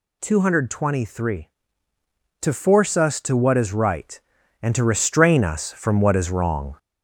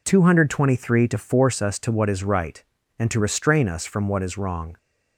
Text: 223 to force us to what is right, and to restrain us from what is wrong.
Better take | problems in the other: second | gets louder; slight; throughout; 3 dB

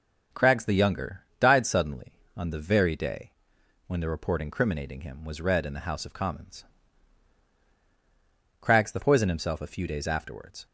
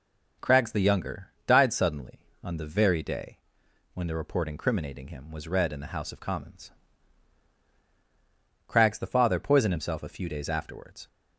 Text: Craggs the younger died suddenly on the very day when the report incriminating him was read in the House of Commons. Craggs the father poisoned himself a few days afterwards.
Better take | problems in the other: second | starts louder than the rest; until 1.5 s; 7 dB // pauses between "younger" and "died"; slight; at 1.2 s; 0.18 s long; slight in the second // pauses between "day" and "when"; noticeable; at 3.3 s; 0.56 s long; noticeable in the second // skips "father"; at 8.9 s

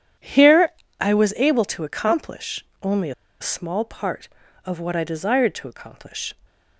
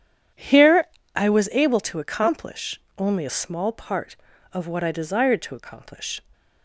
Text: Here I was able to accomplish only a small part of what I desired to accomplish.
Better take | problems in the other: second | pauses between "Here" and "I"; slight; at 0.7 s; 0.28 s long; slight in the second // pauses between "accomplish" and "only"; slight; at 2.6 s; 0.16 s long; slight in the second // pauses between "only" and "a"; slight; at 3.1 s; 0.28 s long

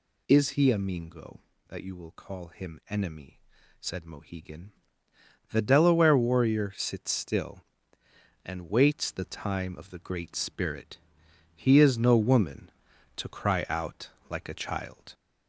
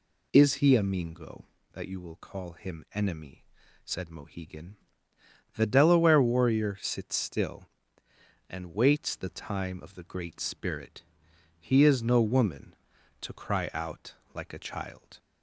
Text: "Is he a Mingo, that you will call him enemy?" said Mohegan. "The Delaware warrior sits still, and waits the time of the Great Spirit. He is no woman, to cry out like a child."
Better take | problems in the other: second | gets louder; slight; throughout; 2.5 dB // pauses between "out" and "like"; slight; at 14.0 s; 0.18 s long; slight in the second

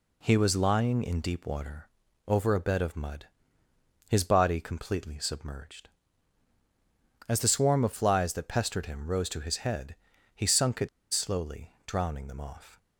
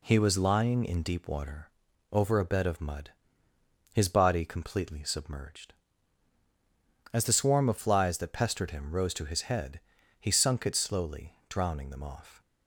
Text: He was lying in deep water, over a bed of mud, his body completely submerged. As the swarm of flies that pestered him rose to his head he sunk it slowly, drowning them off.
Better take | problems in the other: second | pauses between "head" and "he"; at 9.9 s; 0.40 s long; also in the second // pauses between "it" and "slowly"; slight; at 10.8 s; 0.24 s long

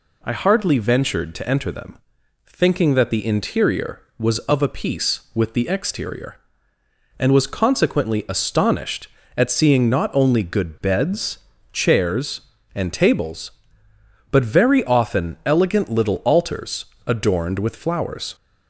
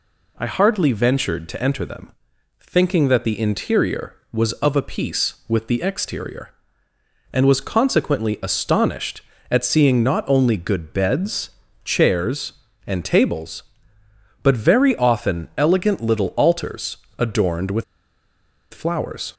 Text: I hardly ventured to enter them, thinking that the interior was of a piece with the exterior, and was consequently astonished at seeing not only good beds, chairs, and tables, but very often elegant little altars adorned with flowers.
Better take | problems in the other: first | pauses between "altars" and "adorned"; slight; at 16.9 s; 0.20 s long; slight in the first // pauses between "with" and "flowers"; noticeable; at 17.8 s; 0.89 s long

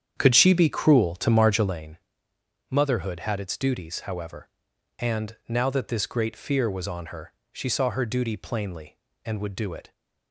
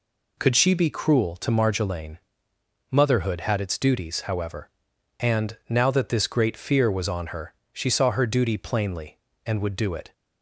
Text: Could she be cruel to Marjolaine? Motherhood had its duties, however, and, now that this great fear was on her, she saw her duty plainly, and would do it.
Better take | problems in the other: second | starts louder than the rest; strong; until 1.8 s; 8.5 dB

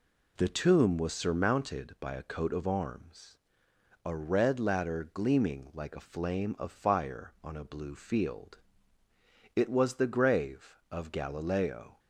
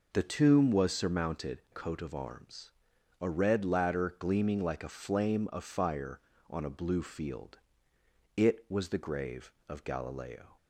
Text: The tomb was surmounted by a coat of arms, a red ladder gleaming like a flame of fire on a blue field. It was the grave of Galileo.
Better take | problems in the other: first | skips "by a"; at 1.6 s

